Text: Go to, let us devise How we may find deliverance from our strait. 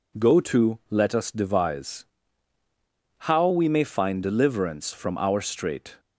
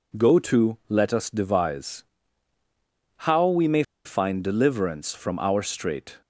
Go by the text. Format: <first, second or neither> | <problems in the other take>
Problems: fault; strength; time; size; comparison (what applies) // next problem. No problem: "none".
first | pauses between "devise" and "How"; at 2.0 s; 1.1 s long; also in the first // pauses between "may" and "find"; slight; at 3.8 s; 0.20 s long